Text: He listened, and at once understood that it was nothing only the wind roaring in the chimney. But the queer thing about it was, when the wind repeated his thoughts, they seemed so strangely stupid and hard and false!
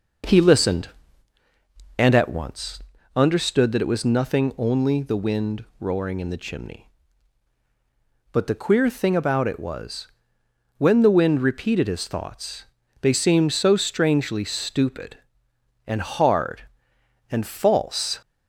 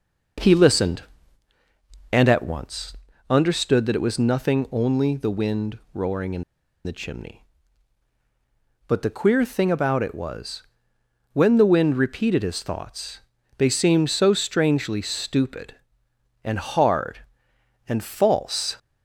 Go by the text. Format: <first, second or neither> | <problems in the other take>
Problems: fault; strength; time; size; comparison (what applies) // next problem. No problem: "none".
first | pauses between "once" and "understood"; slight; at 2.9 s; 0.34 s long; slight in the first // pauses between "in" and "the"; at 6.4 s; 0.42 s long